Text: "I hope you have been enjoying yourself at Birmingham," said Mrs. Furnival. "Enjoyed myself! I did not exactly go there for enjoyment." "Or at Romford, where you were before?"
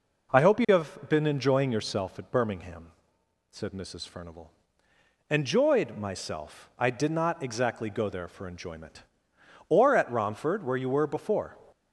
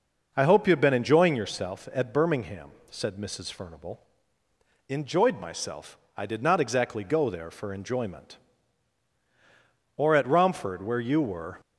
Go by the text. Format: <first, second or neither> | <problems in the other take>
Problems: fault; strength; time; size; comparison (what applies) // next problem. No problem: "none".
first | stops before "before"; at 11.6 s